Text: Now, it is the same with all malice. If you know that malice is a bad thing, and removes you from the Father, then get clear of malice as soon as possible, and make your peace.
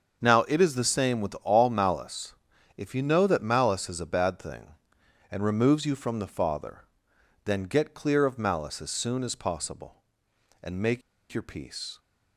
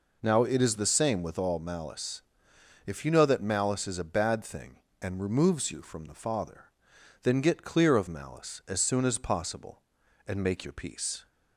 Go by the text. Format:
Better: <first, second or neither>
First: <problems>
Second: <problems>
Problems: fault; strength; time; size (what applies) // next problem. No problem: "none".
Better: second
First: starts louder than the rest; until 1.2 s; 6.5 dB // pauses between "make" and "your"; slight; at 11.0 s; 0.31 s long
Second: none